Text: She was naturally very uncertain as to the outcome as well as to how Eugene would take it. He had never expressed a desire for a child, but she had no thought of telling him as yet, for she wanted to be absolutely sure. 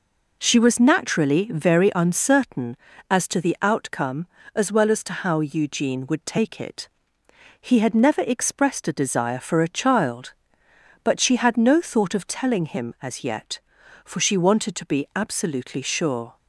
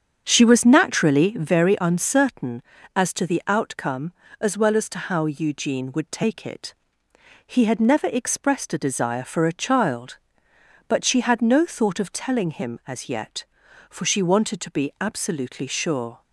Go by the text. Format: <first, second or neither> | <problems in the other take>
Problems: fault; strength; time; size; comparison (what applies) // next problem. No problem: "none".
first | starts louder than the rest; strong; until 1.5 s; 8 dB